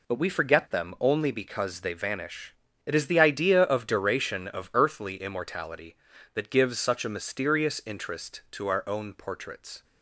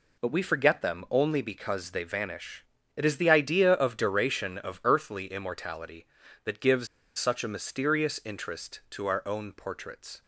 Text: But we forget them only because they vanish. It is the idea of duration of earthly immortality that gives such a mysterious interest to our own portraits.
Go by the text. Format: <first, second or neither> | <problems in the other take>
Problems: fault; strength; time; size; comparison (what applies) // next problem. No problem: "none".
first | pauses between "gives" and "such"; slight; at 6.8 s; 0.31 s long